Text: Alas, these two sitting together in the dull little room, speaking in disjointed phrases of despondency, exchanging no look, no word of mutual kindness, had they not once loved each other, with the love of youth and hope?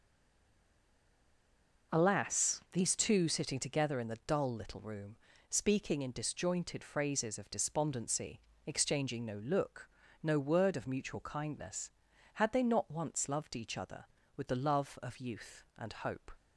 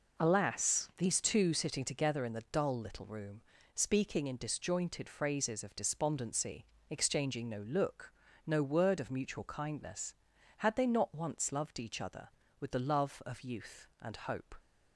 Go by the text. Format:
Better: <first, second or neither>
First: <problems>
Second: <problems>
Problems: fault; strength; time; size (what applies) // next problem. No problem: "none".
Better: second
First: stays silent before the first word; noticeable; until 1.9 s; 1.9 s long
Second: none